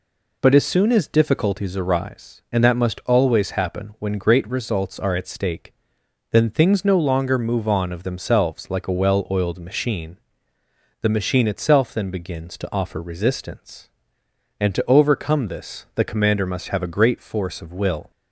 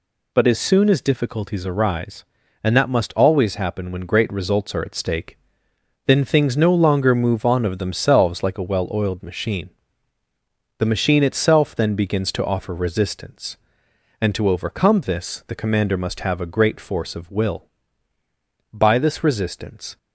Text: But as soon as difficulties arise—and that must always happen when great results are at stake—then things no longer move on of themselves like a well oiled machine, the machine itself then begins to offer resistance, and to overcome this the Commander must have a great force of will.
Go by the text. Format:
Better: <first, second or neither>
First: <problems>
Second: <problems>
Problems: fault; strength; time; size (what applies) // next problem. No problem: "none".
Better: first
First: none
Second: goes on to say "By this resistance"; noticeable; from 18.7 s on; 1.2 s long